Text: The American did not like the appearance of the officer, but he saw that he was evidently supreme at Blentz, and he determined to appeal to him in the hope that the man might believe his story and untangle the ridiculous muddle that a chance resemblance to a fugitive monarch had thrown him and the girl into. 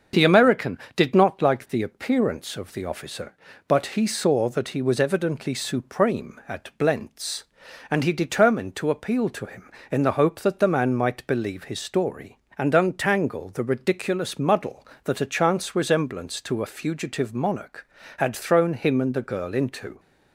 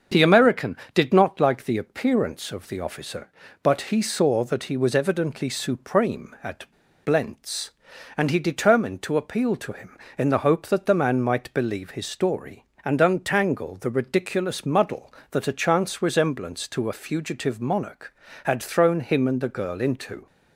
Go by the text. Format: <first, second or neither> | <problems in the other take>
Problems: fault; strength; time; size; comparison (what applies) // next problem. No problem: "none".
first | starts louder than the rest; until 1.2 s; 6.5 dB; also in the first // pauses between "at" and "Blentz"; slight; at 6.7 s; 0.35 s long